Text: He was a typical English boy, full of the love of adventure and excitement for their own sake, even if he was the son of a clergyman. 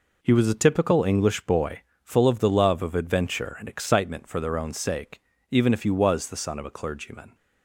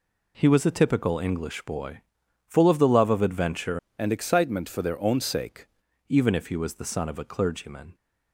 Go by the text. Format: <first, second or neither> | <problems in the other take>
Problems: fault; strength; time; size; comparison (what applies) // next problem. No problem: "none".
first | changes voice from "and" to "sake"; from 3.9 to 5.6 s; 1.7 s long